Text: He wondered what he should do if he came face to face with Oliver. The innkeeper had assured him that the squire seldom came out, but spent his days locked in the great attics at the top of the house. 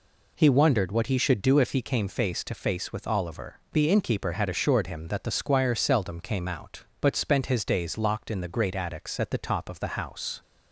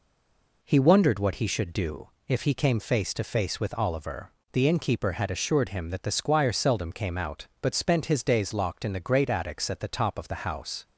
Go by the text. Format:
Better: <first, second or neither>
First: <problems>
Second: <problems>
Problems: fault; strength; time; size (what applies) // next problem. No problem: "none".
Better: first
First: none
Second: stays silent before the first word; slight; until 0.6 s; 0.6 s long // pauses between "do" and "if"; slight; at 2.0 s; 0.18 s long